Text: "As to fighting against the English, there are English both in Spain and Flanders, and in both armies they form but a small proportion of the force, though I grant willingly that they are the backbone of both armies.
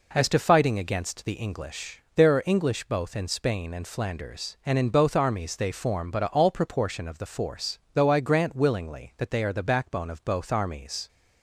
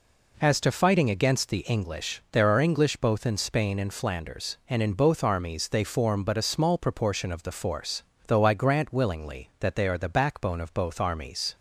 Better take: second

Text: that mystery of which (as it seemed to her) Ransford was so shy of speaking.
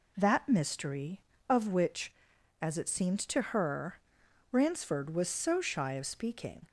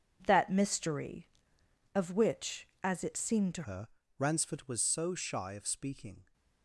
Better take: first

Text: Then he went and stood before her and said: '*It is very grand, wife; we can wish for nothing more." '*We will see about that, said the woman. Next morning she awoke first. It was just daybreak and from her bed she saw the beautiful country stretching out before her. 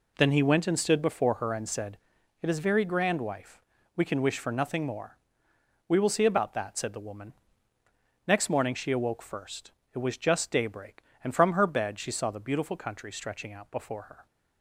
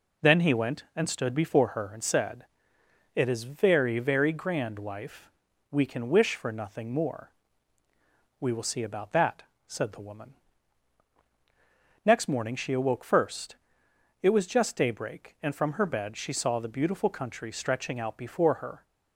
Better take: first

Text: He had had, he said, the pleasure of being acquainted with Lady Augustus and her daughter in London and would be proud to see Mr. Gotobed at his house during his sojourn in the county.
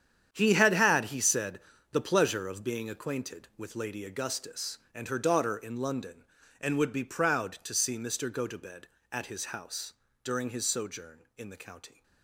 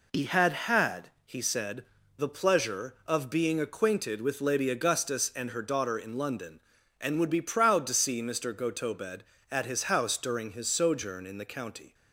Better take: second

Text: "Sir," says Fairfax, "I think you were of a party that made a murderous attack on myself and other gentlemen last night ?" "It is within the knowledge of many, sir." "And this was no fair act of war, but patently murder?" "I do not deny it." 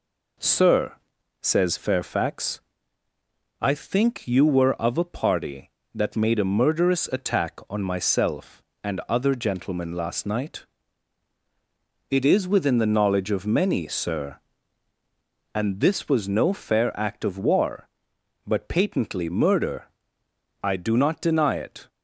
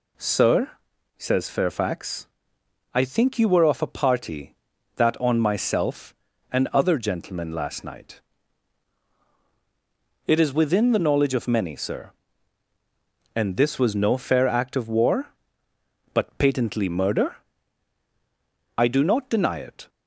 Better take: first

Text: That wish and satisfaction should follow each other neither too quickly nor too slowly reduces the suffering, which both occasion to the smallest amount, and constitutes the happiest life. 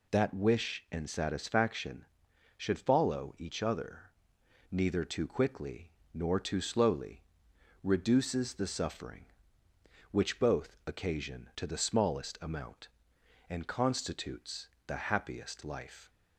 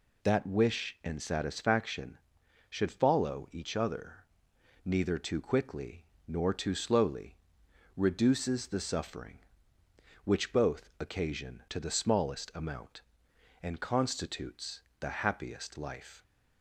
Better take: neither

